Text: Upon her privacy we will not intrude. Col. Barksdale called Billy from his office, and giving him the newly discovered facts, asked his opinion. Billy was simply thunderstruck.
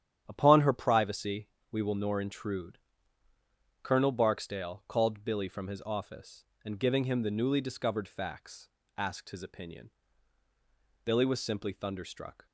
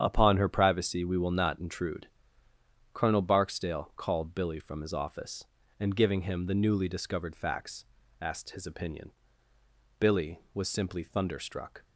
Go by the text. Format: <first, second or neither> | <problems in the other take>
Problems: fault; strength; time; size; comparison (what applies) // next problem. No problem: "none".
second | starts louder than the rest; strong; until 1.2 s; 10 dB; strong in the second // pauses between "privacy" and "we"; slight; at 1.4 s; 0.24 s long // says "nor" for "not"; at 1.9 s